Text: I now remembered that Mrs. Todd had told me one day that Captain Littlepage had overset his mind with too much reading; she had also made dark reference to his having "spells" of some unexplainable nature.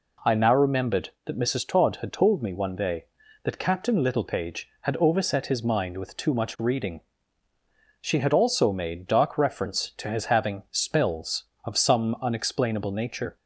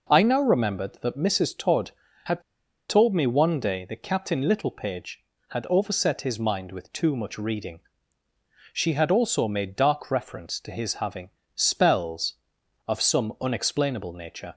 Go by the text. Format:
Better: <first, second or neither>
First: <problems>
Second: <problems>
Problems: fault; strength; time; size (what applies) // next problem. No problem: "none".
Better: first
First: none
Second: pauses between "had" and "told"; noticeable; at 2.4 s; 0.47 s long // pauses between "having" and "spells"; slight; at 11.3 s; 0.26 s long